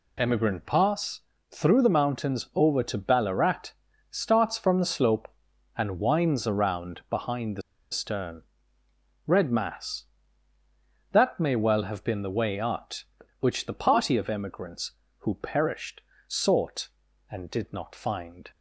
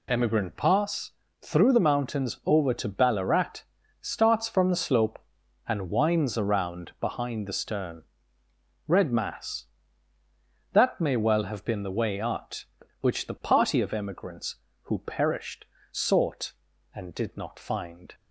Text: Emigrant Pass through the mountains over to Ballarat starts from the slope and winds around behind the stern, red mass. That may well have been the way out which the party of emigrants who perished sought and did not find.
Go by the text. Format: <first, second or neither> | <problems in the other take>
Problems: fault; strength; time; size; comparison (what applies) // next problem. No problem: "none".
second | pauses between "Pass" and "through"; slight; at 1.2 s; 0.28 s long; slight in the second // pauses between "Ballarat" and "starts"; at 3.7 s; 0.40 s long; also in the second // pauses between "the" and "stern"; slight; at 7.6 s; 0.30 s long // pauses between "perished" and "sought"; slight; at 16.0 s; 0.26 s long; slight in the second